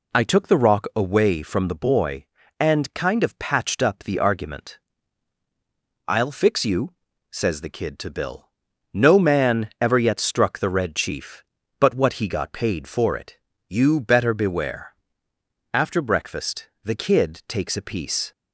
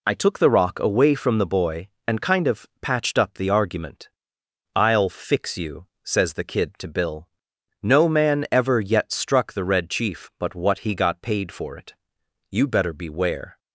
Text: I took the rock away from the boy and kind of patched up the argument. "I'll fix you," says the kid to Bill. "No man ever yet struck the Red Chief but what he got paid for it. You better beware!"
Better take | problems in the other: second | goes on to say "After breakfast the kid takes a piece"; strong; from 15.7 s on; 2.5 s long

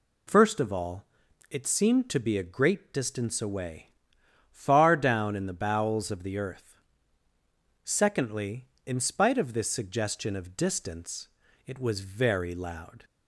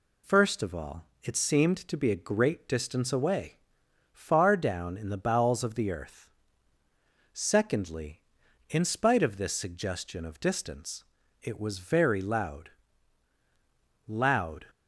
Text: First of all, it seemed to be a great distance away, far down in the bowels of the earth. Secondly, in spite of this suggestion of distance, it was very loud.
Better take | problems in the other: first | says "loud" twice; at 14.0 s

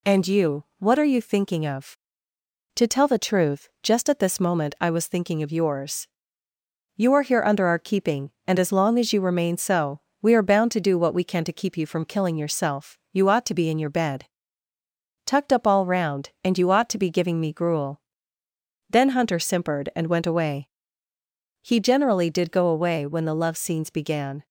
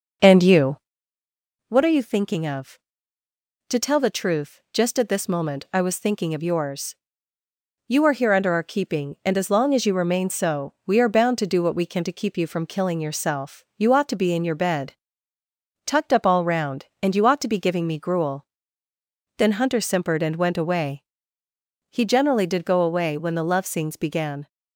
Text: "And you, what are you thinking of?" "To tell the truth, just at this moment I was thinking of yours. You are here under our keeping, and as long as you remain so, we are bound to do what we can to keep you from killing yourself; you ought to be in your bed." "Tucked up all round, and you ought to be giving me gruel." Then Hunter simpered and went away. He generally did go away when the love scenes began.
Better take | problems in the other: first | starts louder than the rest; noticeable; until 1.4 s; 5.5 dB

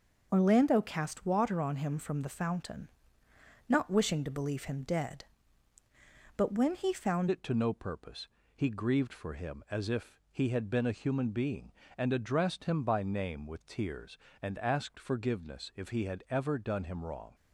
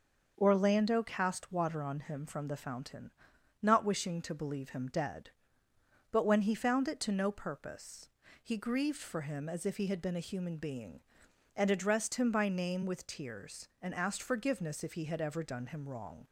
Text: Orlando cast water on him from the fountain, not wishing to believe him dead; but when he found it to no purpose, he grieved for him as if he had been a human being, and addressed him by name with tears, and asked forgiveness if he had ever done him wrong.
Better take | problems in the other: second | starts louder than the rest; noticeable; until 1.3 s; 6 dB; noticeable in the second // changes voice at "it"; from 7.3 s on; 10.0 s long

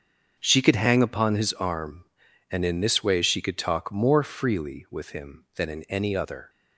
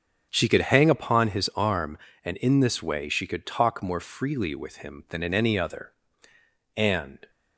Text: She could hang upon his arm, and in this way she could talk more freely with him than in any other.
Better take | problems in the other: first | starts louder than the rest; strong; until 1.3 s; 7 dB; also in the first // goes on to say "And"; from 6.7 s on; 0.54 s long

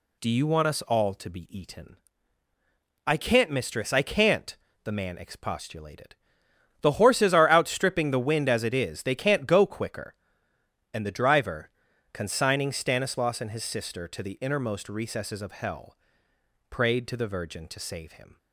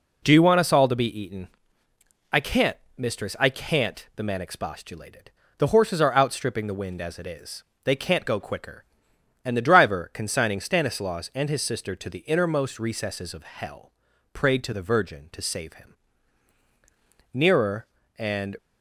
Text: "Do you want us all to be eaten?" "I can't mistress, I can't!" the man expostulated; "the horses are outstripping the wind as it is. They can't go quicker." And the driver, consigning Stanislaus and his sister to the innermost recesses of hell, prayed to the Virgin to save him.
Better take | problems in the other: first | pauses between "can't" and "mistress"; slight; at 2.7 s; 0.18 s long // goes on to say "Nearer and"; noticeable; from 17.3 s on; 1.2 s long

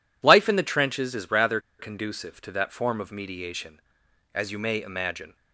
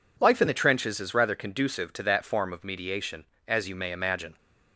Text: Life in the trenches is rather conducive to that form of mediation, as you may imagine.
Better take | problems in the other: second | pauses between "rather" and "conducive"; slight; at 1.5 s; 0.19 s long

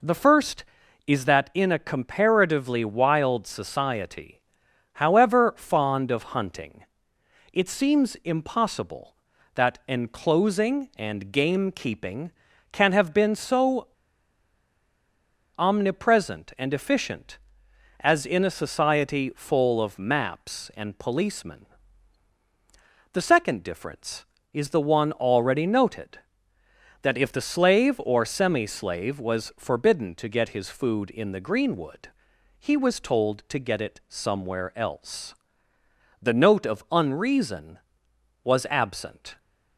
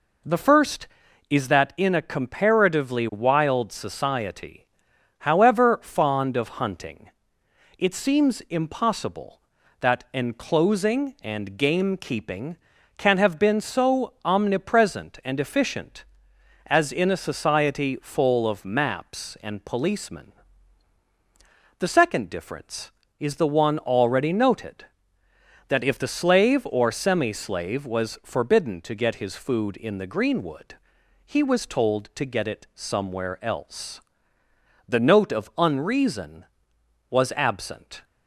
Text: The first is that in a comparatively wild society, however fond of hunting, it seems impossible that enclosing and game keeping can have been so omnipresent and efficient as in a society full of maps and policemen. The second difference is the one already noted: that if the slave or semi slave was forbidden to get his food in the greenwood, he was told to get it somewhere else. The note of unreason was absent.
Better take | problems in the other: second | pauses between "so" and "omnipresent"; strong; at 13.8 s; 1.6 s long

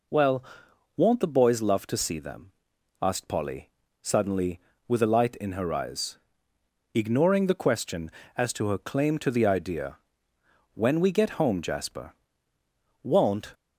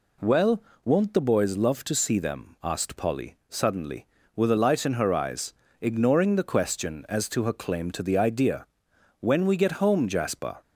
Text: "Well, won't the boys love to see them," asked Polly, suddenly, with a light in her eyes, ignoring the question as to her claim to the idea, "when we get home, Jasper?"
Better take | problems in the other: second | goes on to say "Won't"; from 13.0 s on; 0.50 s long

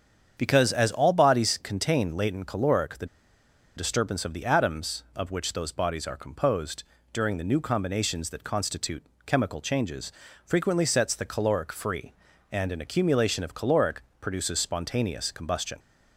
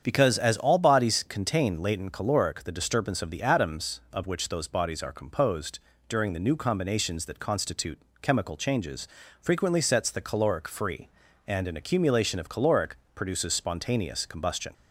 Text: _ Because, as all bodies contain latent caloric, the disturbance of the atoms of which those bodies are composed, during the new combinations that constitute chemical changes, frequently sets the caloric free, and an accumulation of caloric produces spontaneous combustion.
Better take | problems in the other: second | starts louder than the rest; strong; until 1.3 s; 8 dB; strong in the second // pauses between "the" and "disturbance"; noticeable; at 3.0 s; 0.70 s long // pauses between "constitute" and "chemical"; slight; at 9.0 s; 0.22 s long; slight in the second // pauses between "caloric" and "produces"; slight; at 14.0 s; 0.16 s long; slight in the second

